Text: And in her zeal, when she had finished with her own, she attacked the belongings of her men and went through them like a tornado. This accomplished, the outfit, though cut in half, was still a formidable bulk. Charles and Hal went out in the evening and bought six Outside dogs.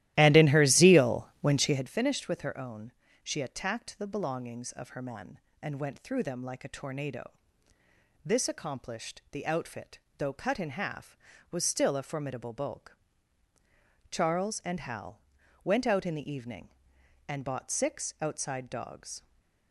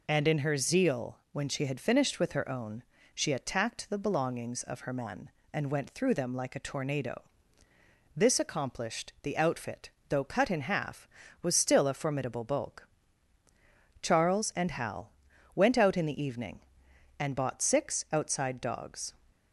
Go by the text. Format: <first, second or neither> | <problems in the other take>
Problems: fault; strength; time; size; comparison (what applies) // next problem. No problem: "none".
second | starts louder than the rest; strong; until 2.0 s; 15 dB // pauses between "Hal" and "went"; at 15.2 s; 0.42 s long; also in the second // stays silent after the last word; slight; from 19.1 s on; 0.6 s long